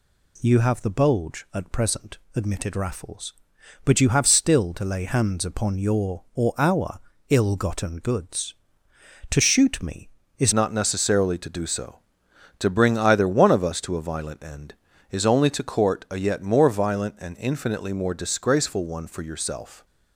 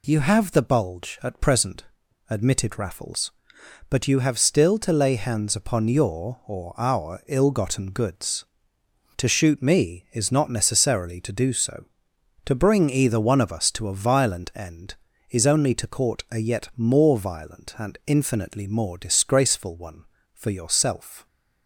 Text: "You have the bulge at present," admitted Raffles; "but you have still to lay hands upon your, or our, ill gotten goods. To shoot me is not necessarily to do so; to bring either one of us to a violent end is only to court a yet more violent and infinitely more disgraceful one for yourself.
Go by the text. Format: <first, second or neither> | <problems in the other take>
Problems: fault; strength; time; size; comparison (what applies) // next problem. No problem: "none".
second | changes voice at "not"; from 10.5 s on; 9.3 s long